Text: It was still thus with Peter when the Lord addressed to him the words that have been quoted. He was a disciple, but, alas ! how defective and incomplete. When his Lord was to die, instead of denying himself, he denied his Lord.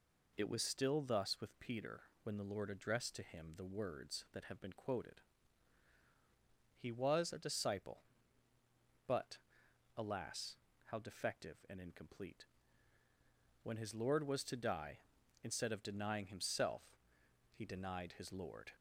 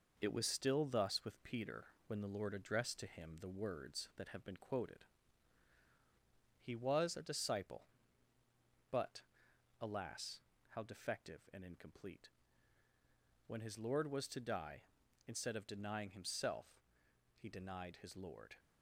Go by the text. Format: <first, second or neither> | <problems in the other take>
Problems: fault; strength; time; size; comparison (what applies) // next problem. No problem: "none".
first | gets quieter; throughout; 3.5 dB // pauses between "Peter" and "when"; slight; at 1.8 s; 0.20 s long; slight in the first